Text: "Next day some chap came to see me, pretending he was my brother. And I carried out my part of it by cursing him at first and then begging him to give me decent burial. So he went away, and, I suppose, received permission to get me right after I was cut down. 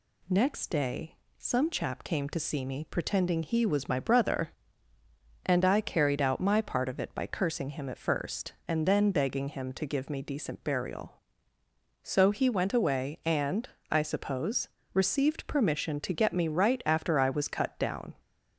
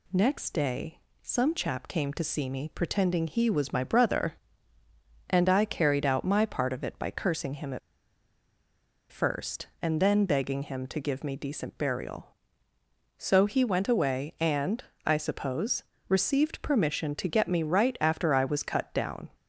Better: first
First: pauses between "day" and "some"; slight; at 1.1 s; 0.21 s long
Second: pauses between "day" and "some"; slight; at 0.9 s; 0.22 s long // pauses between "at" and "first"; strong; at 7.7 s; 1.3 s long

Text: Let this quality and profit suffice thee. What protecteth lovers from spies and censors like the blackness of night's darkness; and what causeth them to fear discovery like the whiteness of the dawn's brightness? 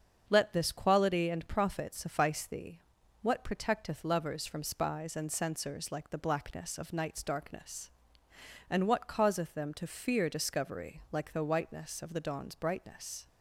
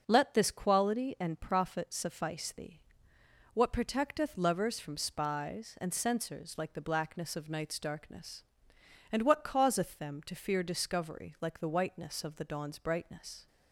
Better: neither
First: starts louder than the rest; until 1.2 s; 7 dB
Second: starts louder than the rest; until 1.0 s; 6.5 dB

